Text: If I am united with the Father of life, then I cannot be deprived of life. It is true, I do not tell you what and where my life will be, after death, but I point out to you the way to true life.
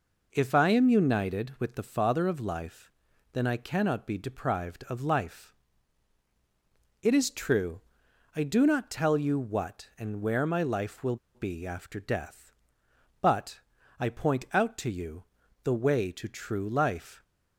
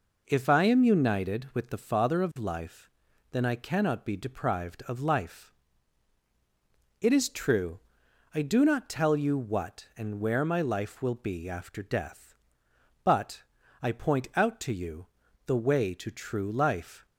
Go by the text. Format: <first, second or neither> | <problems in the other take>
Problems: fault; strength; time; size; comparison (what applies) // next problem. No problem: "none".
second | pauses between "will" and "be"; slight; at 11.1 s; 0.18 s long // pauses between "but" and "I"; at 13.5 s; 0.40 s long; also in the second // pauses between "you" and "the"; at 15.2 s; 0.40 s long; also in the second